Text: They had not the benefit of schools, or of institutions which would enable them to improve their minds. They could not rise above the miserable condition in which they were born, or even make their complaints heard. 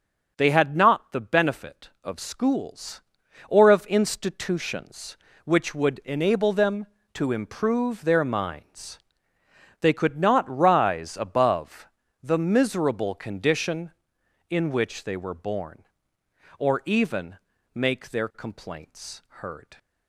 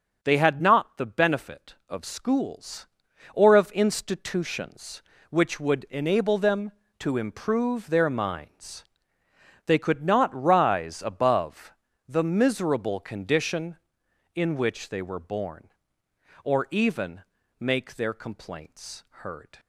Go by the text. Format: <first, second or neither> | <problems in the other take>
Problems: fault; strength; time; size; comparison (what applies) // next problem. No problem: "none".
neither | starts louder than the rest; the same in both // pauses between "above" and "the"; slight; the same in both // pauses between "even" and "make"; the same in both